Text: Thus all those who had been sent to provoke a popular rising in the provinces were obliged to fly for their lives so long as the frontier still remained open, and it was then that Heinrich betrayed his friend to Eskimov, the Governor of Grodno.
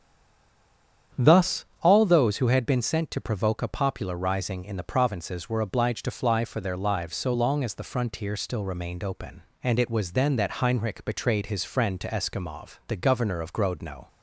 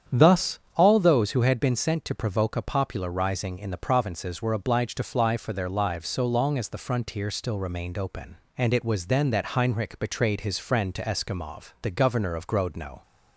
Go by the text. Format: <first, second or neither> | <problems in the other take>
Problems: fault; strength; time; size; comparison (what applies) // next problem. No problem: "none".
second | stays silent before the first word; until 1.1 s; 1.1 s long // starts louder than the rest; strong; until 2.3 s; 8.5 dB; strong in the second // pauses between "Thus" and "all"; slight; at 1.6 s; 0.16 s long; slight in the second